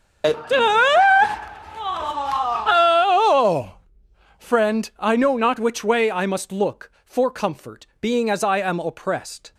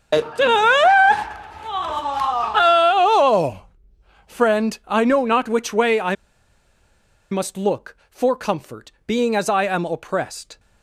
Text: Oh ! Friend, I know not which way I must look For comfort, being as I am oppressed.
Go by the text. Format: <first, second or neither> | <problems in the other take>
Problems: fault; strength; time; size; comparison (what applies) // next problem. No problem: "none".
first | starts louder than the rest; strong; until 3.5 s; 9.5 dB; strong in the first // pauses between "I" and "must"; at 6.1 s; 1.1 s long